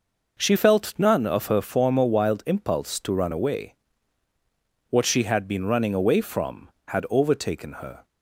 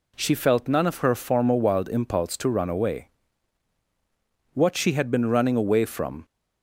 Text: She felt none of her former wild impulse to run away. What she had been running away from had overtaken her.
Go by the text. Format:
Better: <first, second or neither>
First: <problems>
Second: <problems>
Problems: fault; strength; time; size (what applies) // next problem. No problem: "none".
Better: first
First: none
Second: stops before "had overtaken her"; at 6.2 s